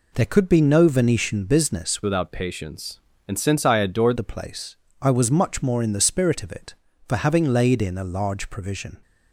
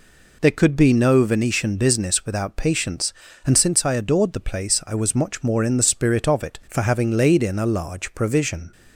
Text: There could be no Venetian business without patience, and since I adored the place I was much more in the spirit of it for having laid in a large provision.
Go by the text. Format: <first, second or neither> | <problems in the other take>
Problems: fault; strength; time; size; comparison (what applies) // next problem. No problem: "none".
second | changes voice from "without" to "adored"; from 2.0 to 4.1 s; 2.1 s long // pauses between "place" and "I"; slight; at 4.7 s; 0.26 s long